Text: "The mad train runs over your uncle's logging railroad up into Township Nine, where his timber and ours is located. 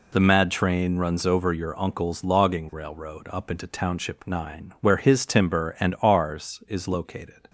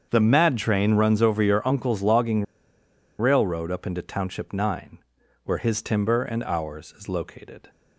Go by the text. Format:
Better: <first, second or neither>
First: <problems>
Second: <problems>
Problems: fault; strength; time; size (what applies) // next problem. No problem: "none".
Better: first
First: none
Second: starts louder than the rest; strong; until 1.1 s; 7.5 dB // pauses between "logging" and "railroad"; noticeable; at 2.4 s; 0.74 s long